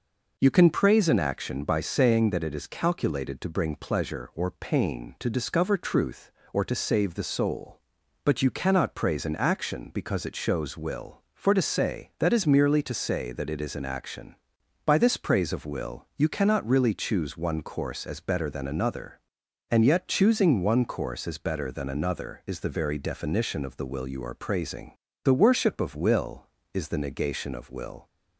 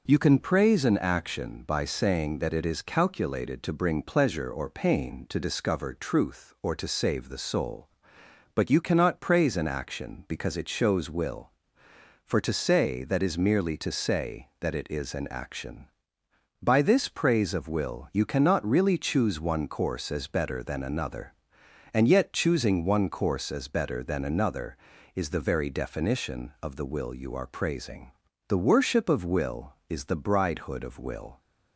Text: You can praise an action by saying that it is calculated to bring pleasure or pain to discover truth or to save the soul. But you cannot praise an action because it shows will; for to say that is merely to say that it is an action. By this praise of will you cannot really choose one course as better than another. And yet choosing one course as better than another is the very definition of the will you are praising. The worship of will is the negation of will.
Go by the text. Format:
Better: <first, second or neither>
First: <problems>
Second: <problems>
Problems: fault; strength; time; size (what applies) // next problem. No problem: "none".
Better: first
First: none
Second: says "bridehood" for "negation"; at 30.1 s